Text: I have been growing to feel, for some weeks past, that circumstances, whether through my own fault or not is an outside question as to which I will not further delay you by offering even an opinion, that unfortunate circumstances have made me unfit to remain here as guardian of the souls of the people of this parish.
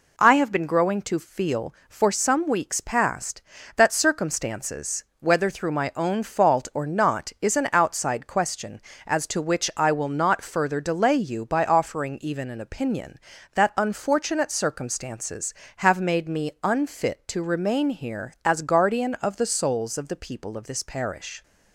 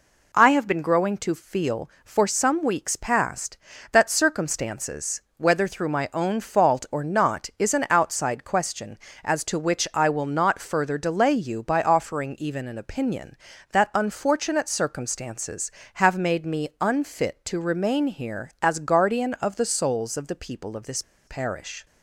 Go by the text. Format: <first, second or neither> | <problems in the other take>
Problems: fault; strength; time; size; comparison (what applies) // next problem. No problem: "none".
first | pauses between "this" and "parish"; slight; at 21.0 s; 0.25 s long